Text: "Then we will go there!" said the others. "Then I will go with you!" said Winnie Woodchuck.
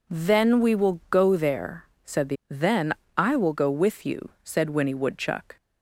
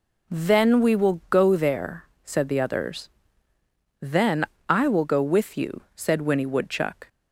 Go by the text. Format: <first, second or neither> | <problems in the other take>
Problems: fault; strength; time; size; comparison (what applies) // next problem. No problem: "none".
second | skips "others"; at 2.4 s // pauses between "Then" and "I"; slight; at 2.9 s; 0.24 s long; slight in the second